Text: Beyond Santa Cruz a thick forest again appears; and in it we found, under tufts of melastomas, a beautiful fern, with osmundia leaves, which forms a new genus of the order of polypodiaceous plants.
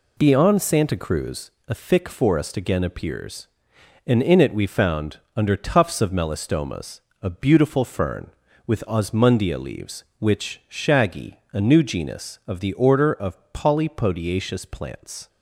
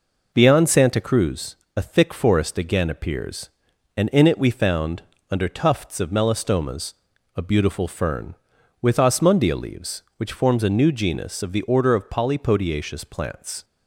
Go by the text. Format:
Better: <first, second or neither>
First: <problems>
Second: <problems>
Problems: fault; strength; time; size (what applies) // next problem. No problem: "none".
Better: second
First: pauses between "Cruz" and "a"; slight; at 1.5 s; 0.16 s long // says "shaggy" for "forms"; at 10.6 s // pauses between "of" and "polypodiaceous"; slight; at 13.3 s; 0.16 s long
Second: pauses between "Cruz" and "a"; slight; at 1.5 s; 0.20 s long